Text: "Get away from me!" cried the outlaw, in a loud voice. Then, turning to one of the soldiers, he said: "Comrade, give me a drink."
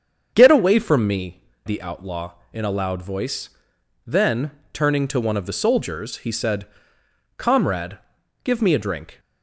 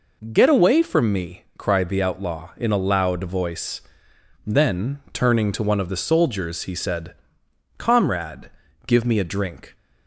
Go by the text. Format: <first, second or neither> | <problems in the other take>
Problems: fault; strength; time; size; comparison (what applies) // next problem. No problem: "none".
second | starts louder than the rest; strong; until 1.3 s; 7 dB // skips "cried"; at 1.5 s